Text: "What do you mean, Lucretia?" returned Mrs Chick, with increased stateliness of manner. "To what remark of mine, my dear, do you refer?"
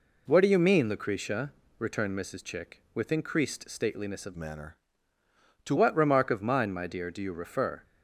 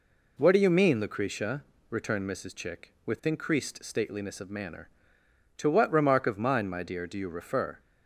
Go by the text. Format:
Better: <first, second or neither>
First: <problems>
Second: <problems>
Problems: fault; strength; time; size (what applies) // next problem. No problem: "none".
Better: second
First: changes voice from "manner" to "To"; from 4.3 to 5.7 s; 1.4 s long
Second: none